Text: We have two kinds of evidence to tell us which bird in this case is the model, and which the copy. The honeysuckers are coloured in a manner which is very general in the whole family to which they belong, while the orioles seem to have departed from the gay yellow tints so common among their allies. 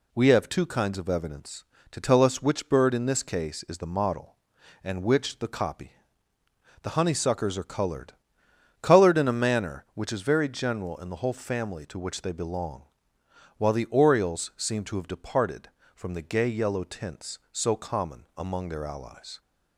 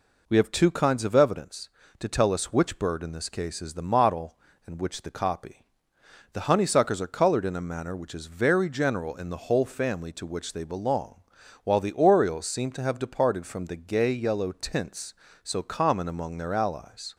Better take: second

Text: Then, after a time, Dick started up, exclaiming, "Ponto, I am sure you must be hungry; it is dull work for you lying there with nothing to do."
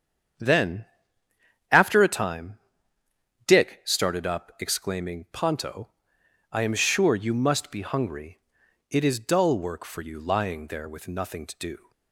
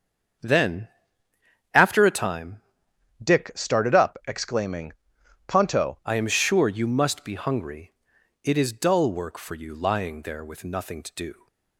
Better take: first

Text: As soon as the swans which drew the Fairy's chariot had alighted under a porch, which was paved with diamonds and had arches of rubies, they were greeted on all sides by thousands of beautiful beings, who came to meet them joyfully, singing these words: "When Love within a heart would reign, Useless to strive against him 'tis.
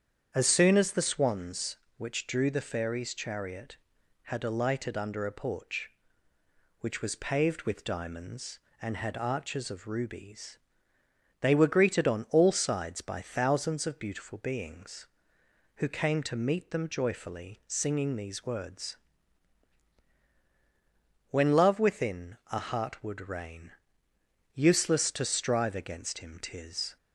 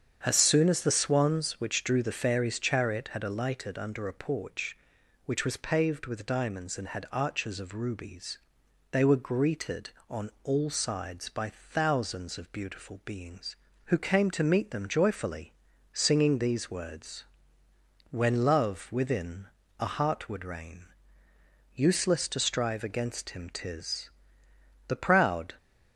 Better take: first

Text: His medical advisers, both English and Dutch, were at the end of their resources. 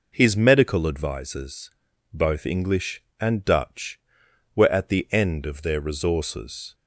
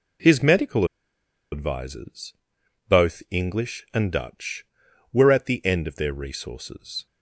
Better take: first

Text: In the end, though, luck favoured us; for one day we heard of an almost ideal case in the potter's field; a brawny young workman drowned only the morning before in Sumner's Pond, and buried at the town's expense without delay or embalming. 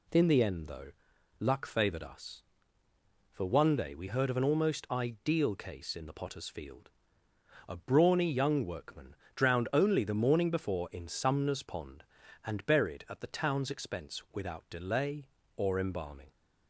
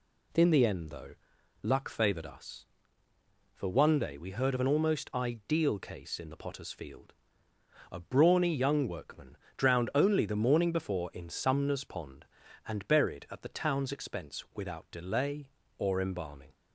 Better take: neither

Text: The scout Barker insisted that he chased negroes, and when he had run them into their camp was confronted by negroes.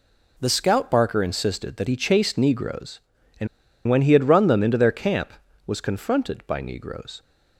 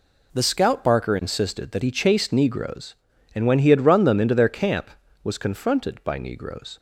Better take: second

